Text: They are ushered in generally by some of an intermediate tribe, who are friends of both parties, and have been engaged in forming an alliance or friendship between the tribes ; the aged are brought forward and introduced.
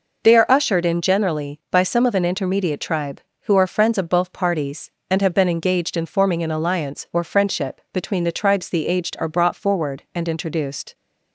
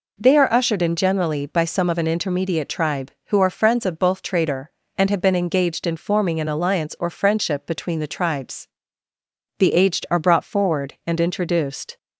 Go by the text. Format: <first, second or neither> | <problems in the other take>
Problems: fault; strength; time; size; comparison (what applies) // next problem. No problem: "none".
first | says "trader" for "parties"; at 4.2 s